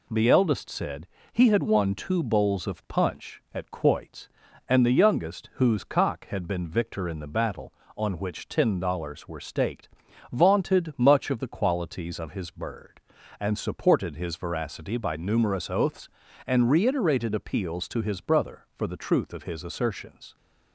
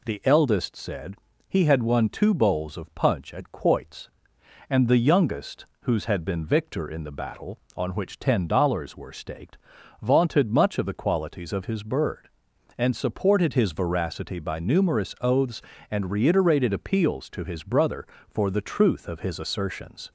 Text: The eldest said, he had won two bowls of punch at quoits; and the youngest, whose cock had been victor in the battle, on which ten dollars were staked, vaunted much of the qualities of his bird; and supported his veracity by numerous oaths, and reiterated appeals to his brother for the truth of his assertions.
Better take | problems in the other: first | skips "cock"; at 6.0 s

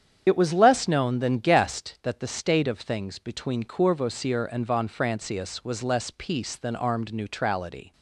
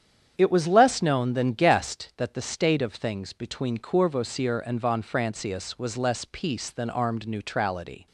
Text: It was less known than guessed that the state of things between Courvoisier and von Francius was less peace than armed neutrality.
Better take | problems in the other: second | loses the start of "It"; at 0.2 s; 30 ms // starts louder than the rest; strong; until 1.2 s; 8.5 dB; strong in the second

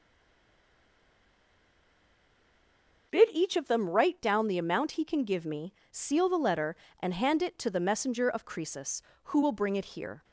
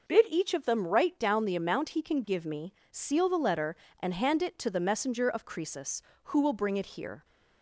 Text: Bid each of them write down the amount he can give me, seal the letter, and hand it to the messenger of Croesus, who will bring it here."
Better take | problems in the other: second | stays silent before the first word; strong; until 3.1 s; 3.1 s long

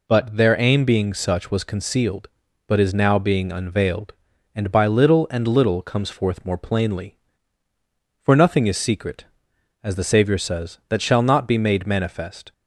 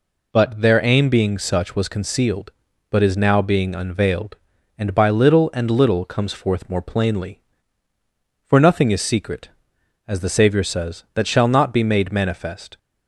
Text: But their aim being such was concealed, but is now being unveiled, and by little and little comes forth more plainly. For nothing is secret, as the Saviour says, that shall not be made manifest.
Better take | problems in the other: neither | none

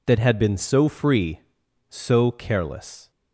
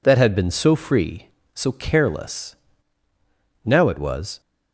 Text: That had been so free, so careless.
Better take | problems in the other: first | goes on to say "Now it was"; noticeable; from 3.6 s on; 0.76 s long

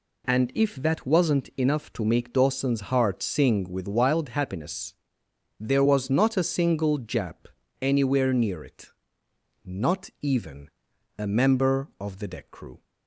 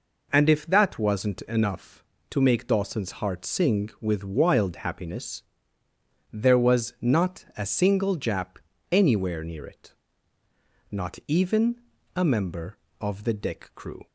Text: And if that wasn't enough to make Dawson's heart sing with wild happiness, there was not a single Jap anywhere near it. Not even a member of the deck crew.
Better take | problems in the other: neither | pauses between "Jap" and "anywhere"; slight; the same in both // pauses between "even" and "a"; the same in both

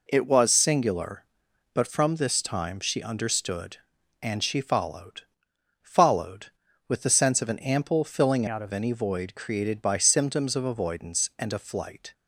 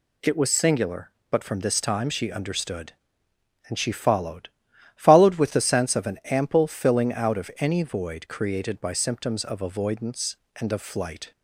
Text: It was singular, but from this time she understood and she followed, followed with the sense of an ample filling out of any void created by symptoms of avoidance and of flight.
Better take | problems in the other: second | changes voice from "out" to "of"; from 8.4 to 8.7 s; 0.3 s long

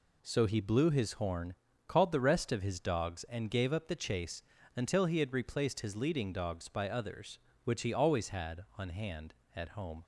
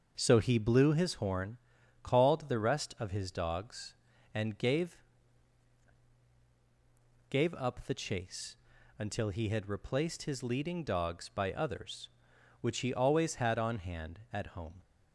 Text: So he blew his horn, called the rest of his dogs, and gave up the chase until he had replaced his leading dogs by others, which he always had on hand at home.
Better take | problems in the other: first | starts louder than the rest; until 1.1 s; 6 dB // says "gave" twice; at 7.2 s // pauses between "chase" and "until"; at 8.5 s; 0.42 s long; slight in the first

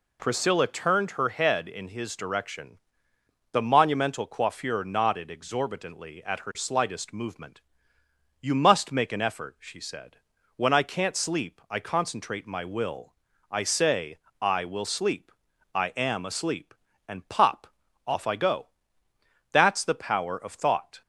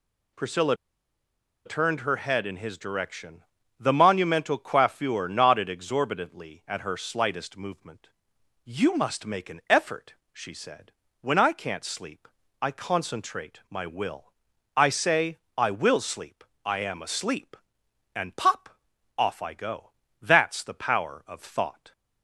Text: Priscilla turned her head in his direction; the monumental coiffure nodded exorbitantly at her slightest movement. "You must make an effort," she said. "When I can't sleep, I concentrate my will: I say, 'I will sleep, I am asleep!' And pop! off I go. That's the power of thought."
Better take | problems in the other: first | pauses between "Priscilla" and "turned"; noticeable; at 0.7 s; 0.90 s long

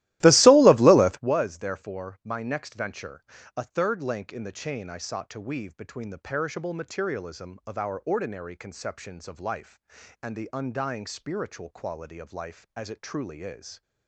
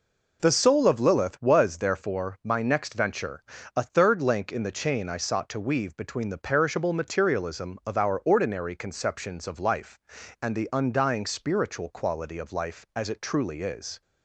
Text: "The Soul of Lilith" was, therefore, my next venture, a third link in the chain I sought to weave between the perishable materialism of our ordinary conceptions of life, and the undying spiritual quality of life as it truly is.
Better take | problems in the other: second | starts louder than the rest; strong; until 1.3 s; 16.5 dB

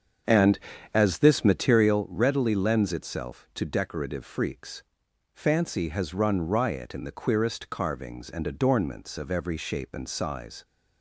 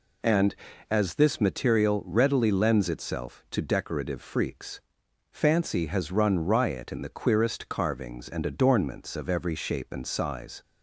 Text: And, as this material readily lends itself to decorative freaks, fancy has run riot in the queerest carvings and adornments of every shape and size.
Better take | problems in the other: second | starts louder than the rest; strong; until 2.1 s; 7 dB

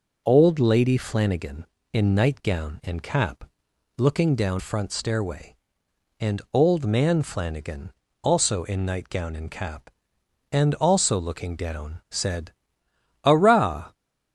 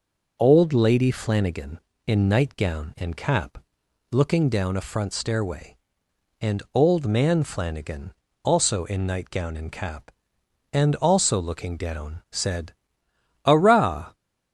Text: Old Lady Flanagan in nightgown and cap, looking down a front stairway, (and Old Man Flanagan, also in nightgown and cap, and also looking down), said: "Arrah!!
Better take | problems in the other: second | skips "a"; at 4.5 s

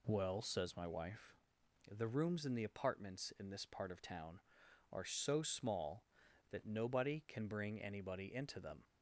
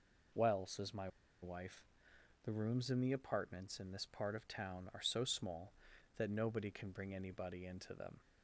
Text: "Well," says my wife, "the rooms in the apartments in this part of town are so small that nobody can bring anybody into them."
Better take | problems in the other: first | pauses between "my" and "wife"; slight; at 1.0 s; 0.34 s long

